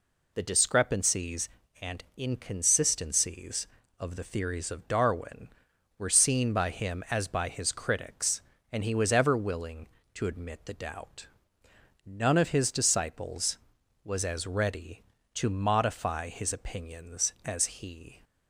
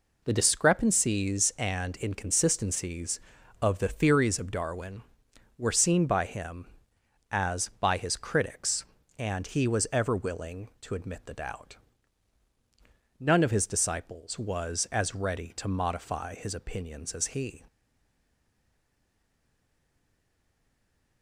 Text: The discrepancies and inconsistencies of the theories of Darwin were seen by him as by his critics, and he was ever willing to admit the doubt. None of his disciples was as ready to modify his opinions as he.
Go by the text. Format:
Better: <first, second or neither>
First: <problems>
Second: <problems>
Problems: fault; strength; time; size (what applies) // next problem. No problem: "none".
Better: first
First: none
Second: stays silent after the last word; strong; from 17.6 s on; 3.6 s long